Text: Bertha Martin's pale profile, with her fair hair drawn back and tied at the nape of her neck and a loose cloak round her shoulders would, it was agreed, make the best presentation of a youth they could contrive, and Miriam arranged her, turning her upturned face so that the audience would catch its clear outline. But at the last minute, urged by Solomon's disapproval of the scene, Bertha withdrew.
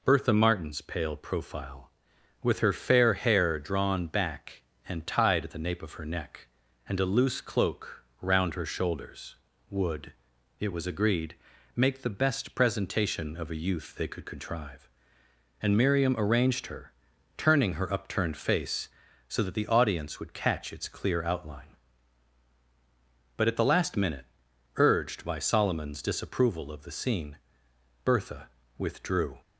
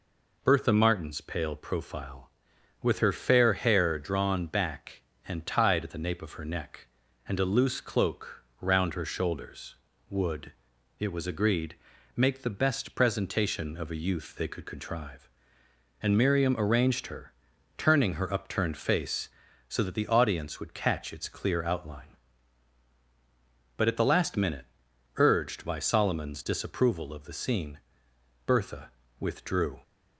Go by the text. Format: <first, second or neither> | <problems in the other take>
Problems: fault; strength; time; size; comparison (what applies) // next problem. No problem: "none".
neither | pauses between "cloak" and "round"; slight; the same in both // pauses between "Bertha" and "withdrew"; slight; the same in both